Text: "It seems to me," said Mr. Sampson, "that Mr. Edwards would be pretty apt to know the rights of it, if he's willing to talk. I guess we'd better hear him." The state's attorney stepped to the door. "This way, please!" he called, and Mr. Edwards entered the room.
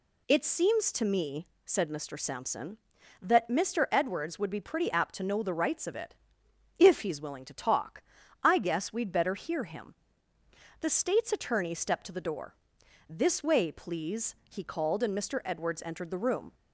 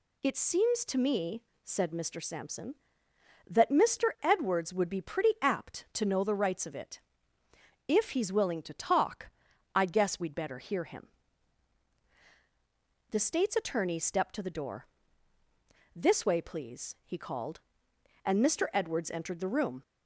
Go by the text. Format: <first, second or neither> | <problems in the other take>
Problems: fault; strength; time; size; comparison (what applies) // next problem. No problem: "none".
neither | none